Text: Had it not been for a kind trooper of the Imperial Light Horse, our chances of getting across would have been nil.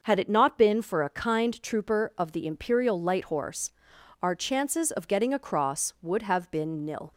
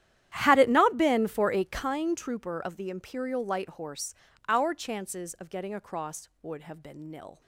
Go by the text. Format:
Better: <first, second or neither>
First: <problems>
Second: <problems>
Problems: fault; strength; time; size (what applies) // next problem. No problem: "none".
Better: first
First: none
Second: starts louder than the rest; strong; until 2.0 s; 11.5 dB